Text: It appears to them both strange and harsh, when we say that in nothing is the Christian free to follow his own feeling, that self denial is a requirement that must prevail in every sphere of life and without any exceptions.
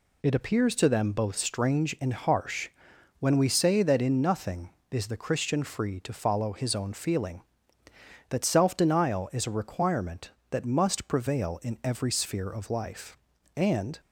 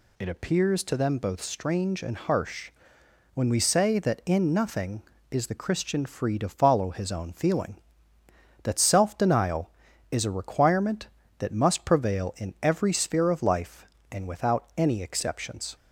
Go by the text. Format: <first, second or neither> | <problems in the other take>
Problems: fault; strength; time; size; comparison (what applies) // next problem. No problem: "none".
second | stops before "without any exceptions"; at 13.9 s